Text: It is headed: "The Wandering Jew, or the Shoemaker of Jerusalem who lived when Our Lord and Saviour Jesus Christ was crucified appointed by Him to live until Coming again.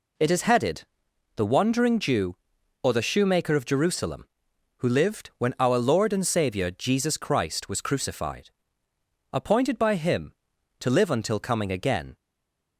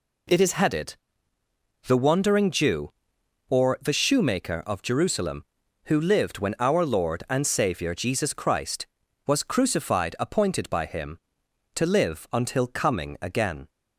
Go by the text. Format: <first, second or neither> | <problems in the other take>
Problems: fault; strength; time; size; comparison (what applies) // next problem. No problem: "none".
second | pauses between "crucified" and "appointed"; noticeable; at 8.4 s; 0.84 s long // stays silent after the last word; slight; from 12.1 s on; 0.6 s long